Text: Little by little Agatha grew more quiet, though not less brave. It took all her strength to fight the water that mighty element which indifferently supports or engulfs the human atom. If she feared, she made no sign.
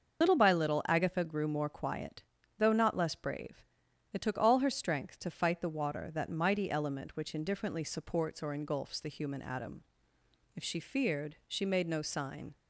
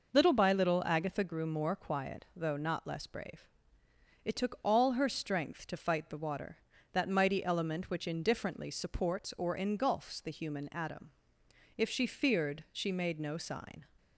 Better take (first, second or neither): second